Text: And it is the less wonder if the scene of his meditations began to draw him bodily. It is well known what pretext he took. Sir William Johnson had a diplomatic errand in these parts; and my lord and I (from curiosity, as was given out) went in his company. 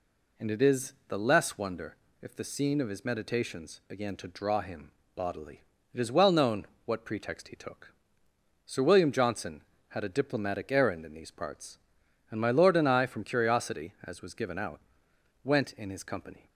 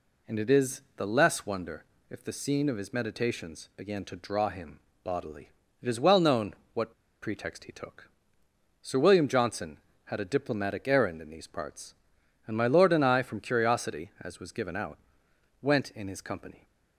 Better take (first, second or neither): first